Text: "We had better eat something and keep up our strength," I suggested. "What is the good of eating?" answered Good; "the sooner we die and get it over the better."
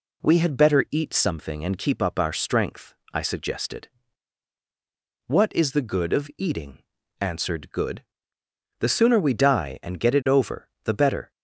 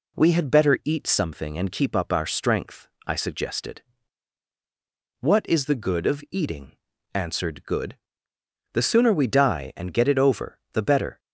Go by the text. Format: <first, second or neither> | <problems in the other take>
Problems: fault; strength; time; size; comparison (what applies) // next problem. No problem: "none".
neither | none